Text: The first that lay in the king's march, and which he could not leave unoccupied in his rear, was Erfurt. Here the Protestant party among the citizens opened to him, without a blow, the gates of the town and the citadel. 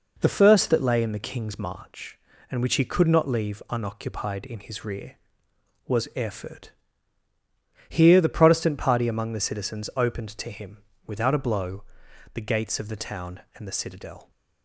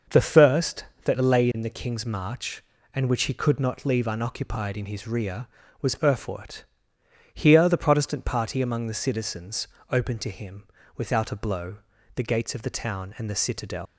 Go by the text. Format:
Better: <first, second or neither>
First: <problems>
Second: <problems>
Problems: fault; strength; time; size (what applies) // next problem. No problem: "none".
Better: first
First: none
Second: starts louder than the rest; noticeable; until 1.3 s; 6 dB // pauses between "citizens" and "opened"; slight; at 9.6 s; 0.22 s long // leaves "citadel" unfinished; at 13.8 s; 125 ms